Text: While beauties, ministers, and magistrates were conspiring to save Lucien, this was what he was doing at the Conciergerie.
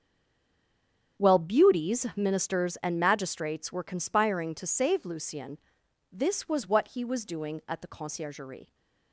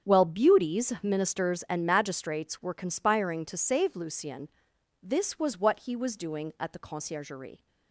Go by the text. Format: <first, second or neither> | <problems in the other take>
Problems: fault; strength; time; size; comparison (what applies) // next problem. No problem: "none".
second | stays silent before the first word; noticeable; until 1.1 s; 1.1 s long // starts louder than the rest; strong; until 2.2 s; 8 dB; strong in the second